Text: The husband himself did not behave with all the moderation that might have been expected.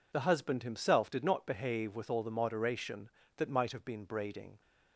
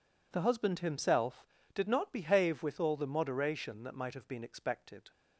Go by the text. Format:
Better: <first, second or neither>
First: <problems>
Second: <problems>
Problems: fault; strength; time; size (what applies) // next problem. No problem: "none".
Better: second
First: says "braiding" for "expected"; at 4.0 s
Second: none